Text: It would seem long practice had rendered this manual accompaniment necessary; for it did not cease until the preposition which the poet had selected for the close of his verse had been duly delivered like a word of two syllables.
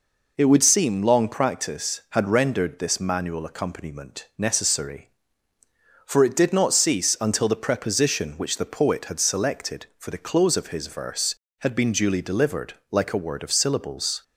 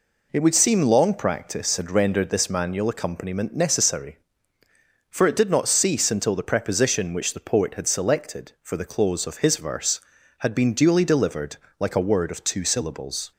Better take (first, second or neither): second